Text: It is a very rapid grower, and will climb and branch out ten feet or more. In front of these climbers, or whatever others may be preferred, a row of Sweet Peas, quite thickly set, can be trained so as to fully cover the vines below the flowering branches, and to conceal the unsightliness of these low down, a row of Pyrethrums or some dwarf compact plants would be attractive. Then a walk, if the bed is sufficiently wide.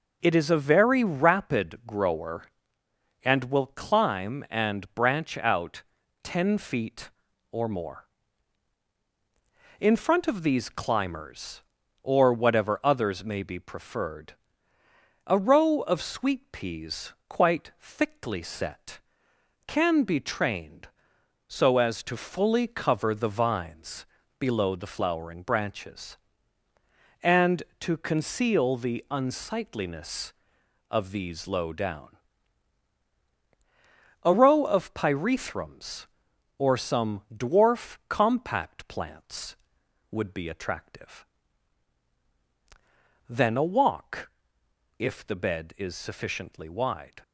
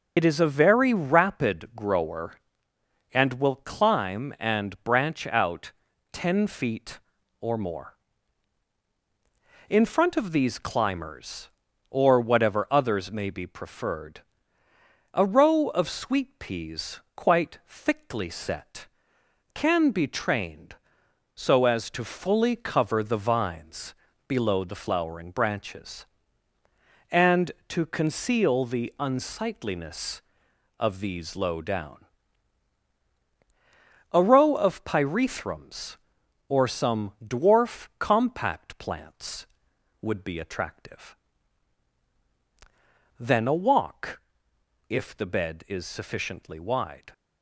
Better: first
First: pauses between "out" and "ten"; at 5.8 s; 0.40 s long // pauses between "vines" and "below"; slight; at 24.0 s; 0.34 s long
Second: loses the start of "It"; at 0.1 s; 55 ms // pauses between "out" and "ten"; at 5.7 s; 0.40 s long // pauses between "vines" and "below"; slight; at 23.9 s; 0.34 s long

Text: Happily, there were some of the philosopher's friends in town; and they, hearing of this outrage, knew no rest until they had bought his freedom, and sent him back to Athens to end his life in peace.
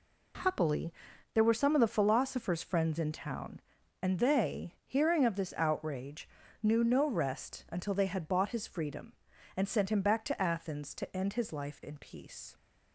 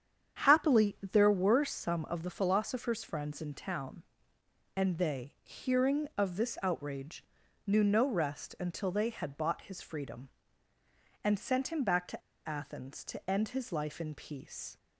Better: first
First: none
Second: starts louder than the rest; strong; until 1.4 s; 8.5 dB // pauses between "to" and "Athens"; slight; at 12.2 s; 0.26 s long

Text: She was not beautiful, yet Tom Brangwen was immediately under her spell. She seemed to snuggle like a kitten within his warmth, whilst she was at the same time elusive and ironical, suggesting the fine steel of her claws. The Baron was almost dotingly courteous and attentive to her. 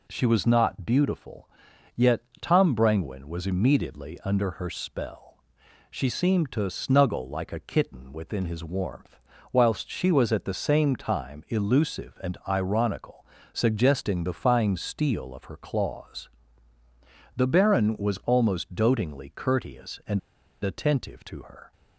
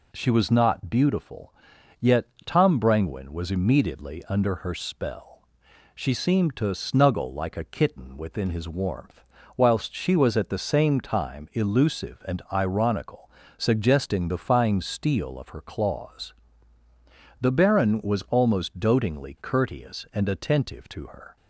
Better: second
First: pauses between "yet" and "Tom"; slight; at 2.2 s; 0.18 s long // pauses between "and" and "attentive"; at 20.1 s; 0.43 s long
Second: pauses between "yet" and "Tom"; slight; at 2.2 s; 0.18 s long

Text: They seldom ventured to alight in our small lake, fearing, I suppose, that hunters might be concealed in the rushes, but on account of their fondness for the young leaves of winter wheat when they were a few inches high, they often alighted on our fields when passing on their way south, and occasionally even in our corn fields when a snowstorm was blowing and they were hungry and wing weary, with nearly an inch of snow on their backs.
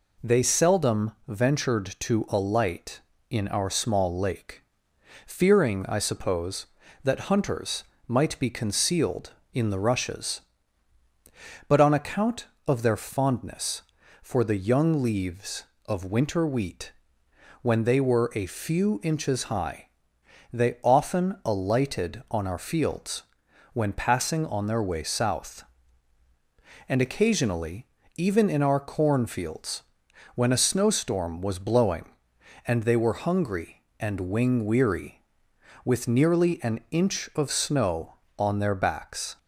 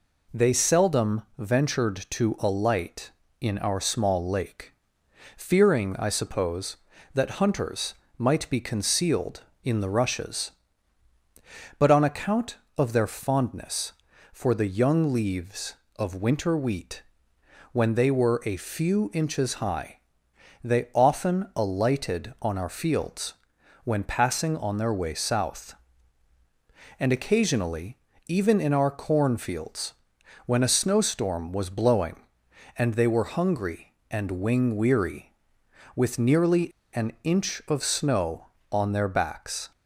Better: first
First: pauses between "seldom" and "ventured"; slight; at 1.1 s; 0.18 s long // pauses between "hunters" and "might"; slight; at 7.8 s; 0.20 s long // pauses between "wheat" and "when"; noticeable; at 16.9 s; 0.70 s long // pauses between "fields" and "when"; noticeable; at 23.2 s; 0.50 s long // pauses between "occasionally" and "even"; slight; at 27.8 s; 0.30 s long // pauses between "fields" and "when"; noticeable; at 29.8 s; 0.52 s long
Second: pauses between "seldom" and "ventured"; slight; at 1.2 s; 0.18 s long // pauses between "hunters" and "might"; slight; at 7.9 s; 0.20 s long // pauses between "wheat" and "when"; noticeable; at 17.0 s; 0.70 s long // pauses between "fields" and "when"; noticeable; at 23.3 s; 0.50 s long // pauses between "occasionally" and "even"; slight; at 27.9 s; 0.30 s long // pauses between "fields" and "when"; noticeable; at 29.9 s; 0.52 s long // pauses between "nearly" and "an"; slight; at 36.7 s; 0.21 s long

